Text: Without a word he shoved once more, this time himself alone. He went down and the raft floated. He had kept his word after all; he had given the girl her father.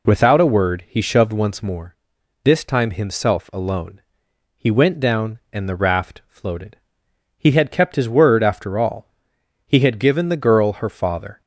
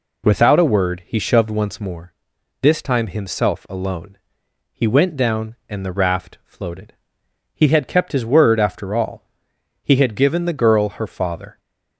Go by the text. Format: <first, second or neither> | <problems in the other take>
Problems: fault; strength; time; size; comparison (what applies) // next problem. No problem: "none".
neither | none